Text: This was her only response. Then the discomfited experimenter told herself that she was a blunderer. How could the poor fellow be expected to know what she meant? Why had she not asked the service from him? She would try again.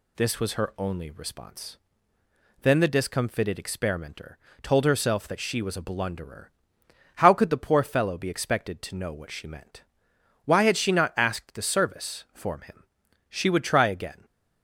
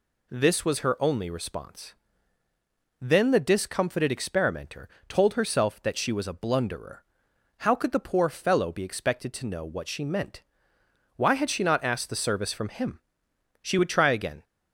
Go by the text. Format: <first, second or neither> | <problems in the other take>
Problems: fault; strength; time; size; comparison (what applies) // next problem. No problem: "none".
second | pauses between "experimenter" and "told"; slight; at 4.3 s; 0.24 s long; slight in the second // says "form" for "from"; at 12.3 s